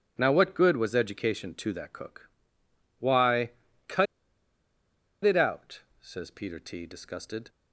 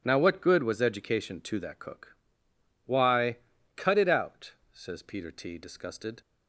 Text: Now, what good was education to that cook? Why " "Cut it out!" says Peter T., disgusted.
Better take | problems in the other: second | starts louder than the rest; strong; until 1.1 s; 7.5 dB; strong in the second // pauses between "Cut" and "it"; at 4.0 s; 1.1 s long

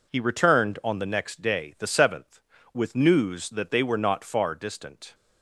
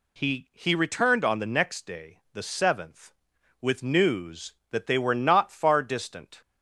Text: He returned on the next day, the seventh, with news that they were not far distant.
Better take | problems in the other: first | says "He" twice; at 0.5 s

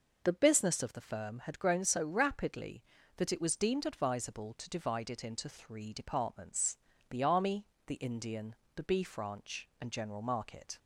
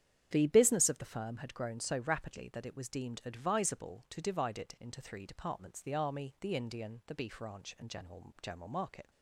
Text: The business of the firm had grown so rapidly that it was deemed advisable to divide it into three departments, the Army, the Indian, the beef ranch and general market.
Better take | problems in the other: first | starts louder than the rest; strong; until 1.3 s; 9.5 dB // says "general" twice; at 8.3 s

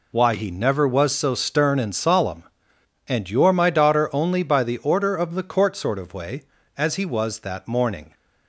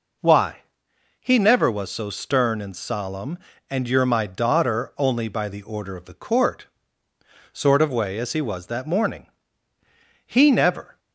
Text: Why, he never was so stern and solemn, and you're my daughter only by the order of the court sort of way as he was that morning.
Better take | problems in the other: first | pauses between "court" and "sort"; noticeable; at 6.6 s; 0.86 s long // goes on to say "He never"; noticeable; from 10.2 s on; 0.74 s long

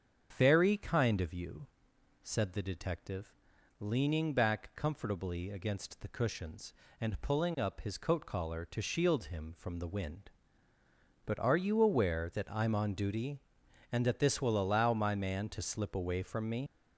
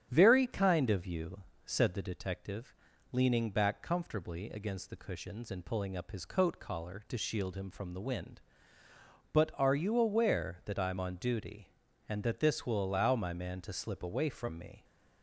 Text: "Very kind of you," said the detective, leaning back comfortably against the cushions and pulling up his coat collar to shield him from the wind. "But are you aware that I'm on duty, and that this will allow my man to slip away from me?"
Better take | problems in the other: second | starts louder than the rest; strong; until 1.3 s; 7.5 dB; strong in the second // leaves "me" unfinished; at 16.6 s; 70 ms

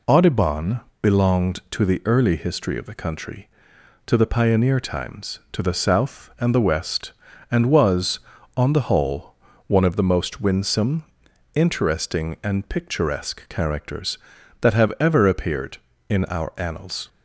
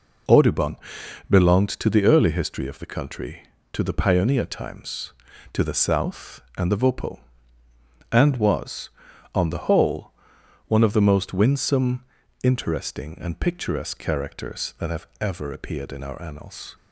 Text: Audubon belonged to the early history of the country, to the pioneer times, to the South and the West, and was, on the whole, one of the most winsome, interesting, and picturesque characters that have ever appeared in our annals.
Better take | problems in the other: first | pauses between "Audubon" and "belonged"; noticeable; at 0.7 s; 0.54 s long; slight in the first // says "Vopo" for "West"; at 6.7 s

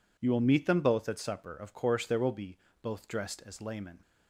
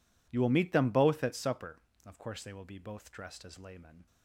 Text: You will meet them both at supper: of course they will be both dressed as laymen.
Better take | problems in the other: second | says "there" for "they"; at 2.0 s // pauses between "be" and "both"; slight; at 2.5 s; 0.24 s long

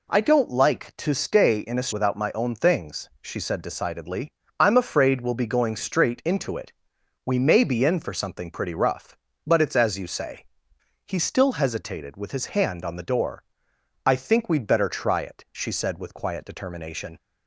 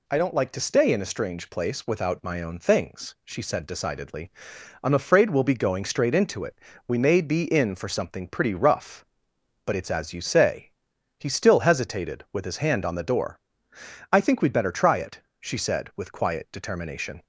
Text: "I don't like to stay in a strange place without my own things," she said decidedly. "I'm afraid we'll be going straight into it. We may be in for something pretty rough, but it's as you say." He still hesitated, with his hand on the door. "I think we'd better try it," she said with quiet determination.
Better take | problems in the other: second | skips "strange place"; at 1.9 s

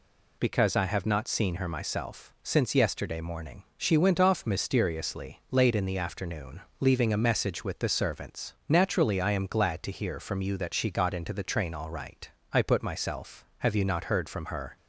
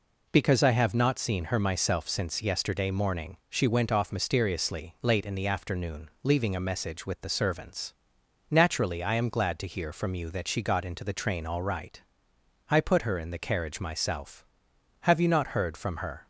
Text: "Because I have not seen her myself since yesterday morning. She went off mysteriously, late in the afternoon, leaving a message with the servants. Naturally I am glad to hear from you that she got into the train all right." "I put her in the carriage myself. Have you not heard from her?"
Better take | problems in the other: second | skips "her in the carriage"; at 12.8 s

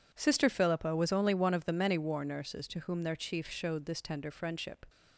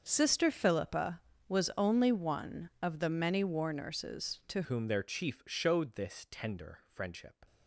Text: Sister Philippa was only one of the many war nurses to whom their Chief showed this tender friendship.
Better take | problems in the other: first | starts louder than the rest; until 1.0 s; 6.5 dB // changes voice at "whom"; from 4.6 s on; 2.8 s long

